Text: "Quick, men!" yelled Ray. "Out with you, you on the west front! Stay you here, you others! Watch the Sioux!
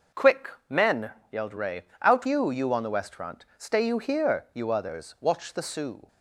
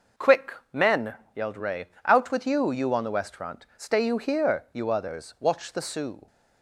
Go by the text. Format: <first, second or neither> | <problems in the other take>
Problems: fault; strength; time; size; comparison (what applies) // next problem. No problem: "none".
second | starts louder than the rest; noticeable; until 1.5 s; 6 dB // skips "with"; at 2.2 s